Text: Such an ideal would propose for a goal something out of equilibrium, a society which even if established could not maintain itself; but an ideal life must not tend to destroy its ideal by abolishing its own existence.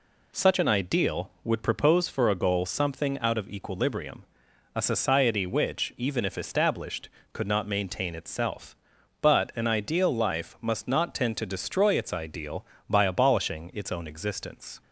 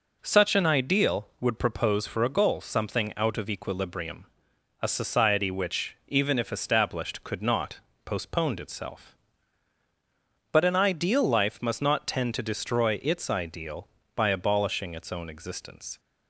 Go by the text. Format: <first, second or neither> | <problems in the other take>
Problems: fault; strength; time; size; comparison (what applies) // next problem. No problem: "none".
first | says "postponed" for "maintain"; at 8.0 s